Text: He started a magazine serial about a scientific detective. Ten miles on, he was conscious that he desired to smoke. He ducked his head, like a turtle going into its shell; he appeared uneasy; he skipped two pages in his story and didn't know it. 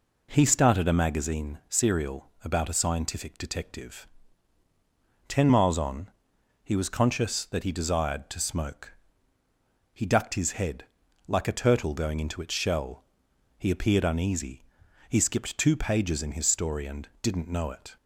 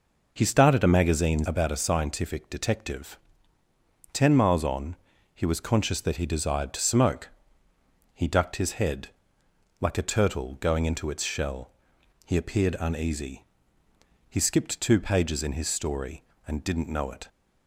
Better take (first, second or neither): first